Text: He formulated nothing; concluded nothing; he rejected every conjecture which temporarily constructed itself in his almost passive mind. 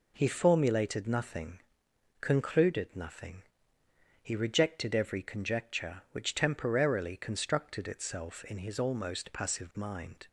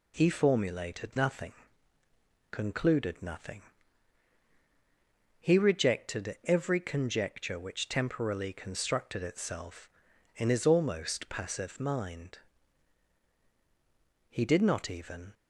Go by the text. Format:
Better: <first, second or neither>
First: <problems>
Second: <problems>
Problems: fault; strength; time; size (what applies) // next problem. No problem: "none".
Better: first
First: none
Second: goes on to say "He did not even"; noticeable; from 14.2 s on; 1.0 s long